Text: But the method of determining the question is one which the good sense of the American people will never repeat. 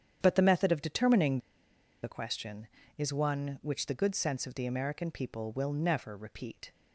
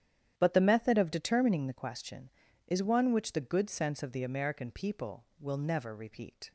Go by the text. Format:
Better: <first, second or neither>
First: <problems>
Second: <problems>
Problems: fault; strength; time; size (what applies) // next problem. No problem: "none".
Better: second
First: starts louder than the rest; strong; until 1.2 s; 9 dB // pauses between "determining" and "the"; noticeable; at 1.3 s; 0.63 s long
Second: starts louder than the rest; strong; until 1.3 s; 10 dB